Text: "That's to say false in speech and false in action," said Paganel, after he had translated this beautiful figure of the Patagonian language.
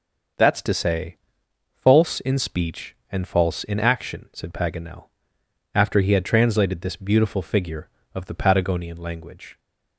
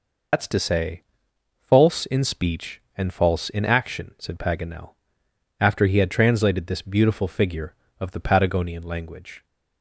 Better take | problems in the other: first | loses the start of "That's"; at 0.3 s; 110 ms // pauses between "say" and "false"; noticeable; at 1.0 s; 0.56 s long; noticeable in the first

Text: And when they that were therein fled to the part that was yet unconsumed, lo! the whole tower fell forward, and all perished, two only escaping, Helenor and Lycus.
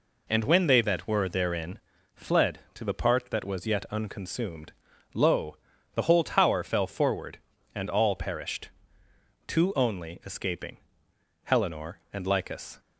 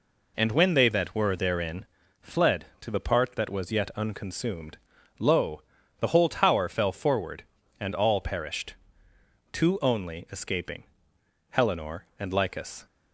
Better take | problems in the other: neither | pauses between "therein" and "fled"; slight; the same in both

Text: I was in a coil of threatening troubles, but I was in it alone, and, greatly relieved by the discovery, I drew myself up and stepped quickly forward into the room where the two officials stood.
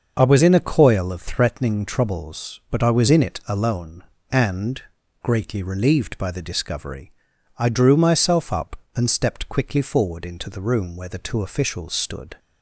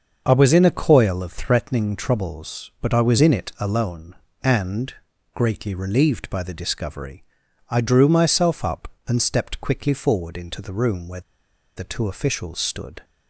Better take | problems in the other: first | starts louder than the rest; until 1.2 s; 6.5 dB; also in the first // pauses between "where" and "the"; noticeable; at 11.2 s; 0.54 s long

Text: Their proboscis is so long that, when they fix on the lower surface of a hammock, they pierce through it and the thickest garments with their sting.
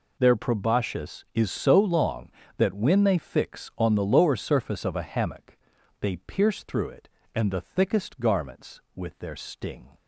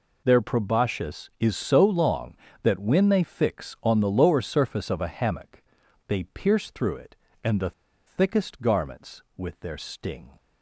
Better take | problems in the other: first | pauses between "the" and "thickest"; slight; at 7.7 s; 0.35 s long

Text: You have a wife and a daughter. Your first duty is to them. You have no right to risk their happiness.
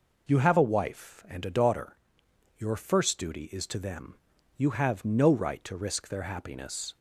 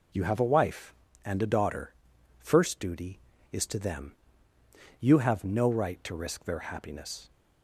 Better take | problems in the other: first | skips "Your"; at 2.1 s

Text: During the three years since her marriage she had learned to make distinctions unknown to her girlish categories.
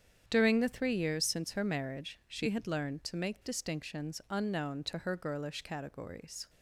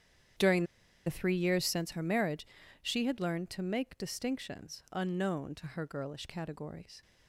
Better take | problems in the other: first | starts louder than the rest; strong; until 1.7 s; 9.5 dB; strong in the first // pauses between "During" and "the"; at 0.6 s; 0.40 s long // pauses between "marriage" and "she"; at 2.4 s; 0.38 s long

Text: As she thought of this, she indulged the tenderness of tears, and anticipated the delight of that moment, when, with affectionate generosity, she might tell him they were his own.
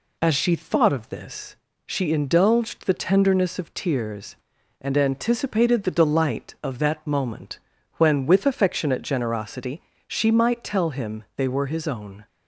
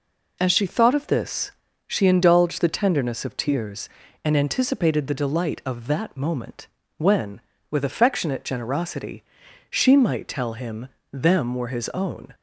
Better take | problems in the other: first | says "them" for "they"; at 11.1 s

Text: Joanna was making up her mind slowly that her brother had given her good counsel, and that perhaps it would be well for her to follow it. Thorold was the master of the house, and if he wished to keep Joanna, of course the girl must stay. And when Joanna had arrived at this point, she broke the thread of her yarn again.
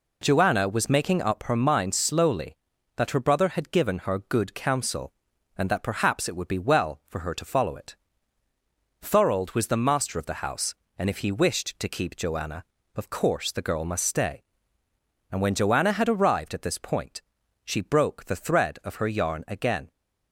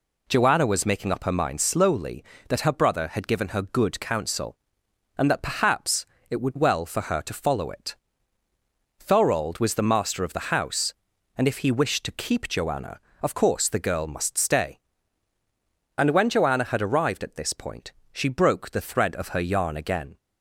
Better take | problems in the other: first | pauses between "perhaps" and "it"; slight; at 6.0 s; 0.24 s long // skips "be"; at 6.5 s

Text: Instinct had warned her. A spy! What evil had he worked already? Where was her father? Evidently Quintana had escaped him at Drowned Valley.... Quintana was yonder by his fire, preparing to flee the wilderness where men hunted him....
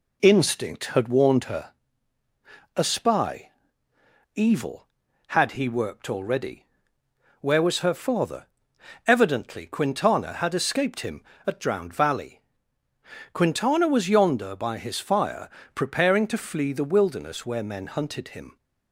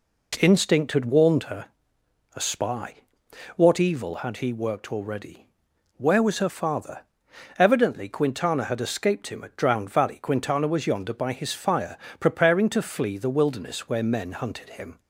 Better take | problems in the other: second | skips "What"; at 3.9 s

